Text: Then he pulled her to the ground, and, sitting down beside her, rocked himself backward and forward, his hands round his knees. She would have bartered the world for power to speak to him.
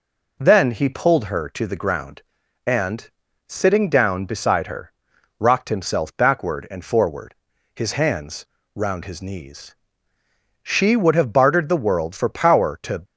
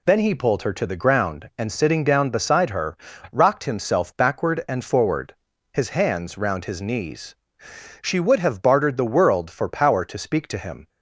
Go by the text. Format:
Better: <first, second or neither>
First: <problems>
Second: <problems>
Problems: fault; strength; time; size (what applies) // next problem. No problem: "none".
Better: second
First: pauses between "hands" and "round"; slight; at 8.4 s; 0.30 s long // stops before "speak to him"; at 13.0 s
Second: none